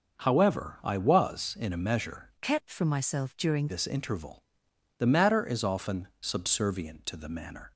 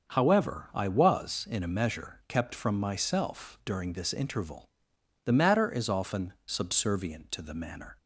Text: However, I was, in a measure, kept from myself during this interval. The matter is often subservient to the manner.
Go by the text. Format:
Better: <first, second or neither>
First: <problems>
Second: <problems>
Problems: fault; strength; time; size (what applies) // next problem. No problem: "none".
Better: second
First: starts louder than the rest; until 1.2 s; 6 dB // changes voice from "kept" to "during"; from 2.4 to 3.6 s; 1.2 s long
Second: starts louder than the rest; until 1.1 s; 6.5 dB